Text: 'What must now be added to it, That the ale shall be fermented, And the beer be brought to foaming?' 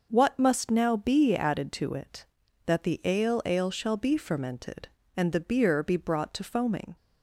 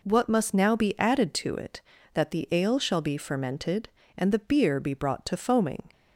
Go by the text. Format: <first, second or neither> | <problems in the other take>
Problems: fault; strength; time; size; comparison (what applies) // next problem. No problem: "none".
second | says "ale" twice; at 3.4 s